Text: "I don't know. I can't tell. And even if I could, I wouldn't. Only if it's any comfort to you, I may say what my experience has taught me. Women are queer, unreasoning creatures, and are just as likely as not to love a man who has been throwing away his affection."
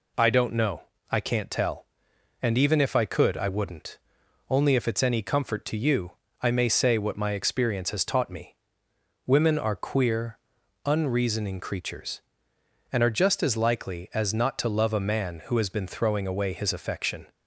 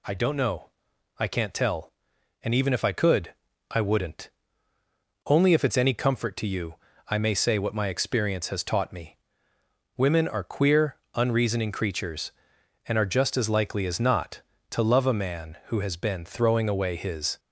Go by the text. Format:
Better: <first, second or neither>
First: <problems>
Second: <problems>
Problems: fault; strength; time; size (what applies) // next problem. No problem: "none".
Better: first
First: none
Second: stops before "affection"; at 17.3 s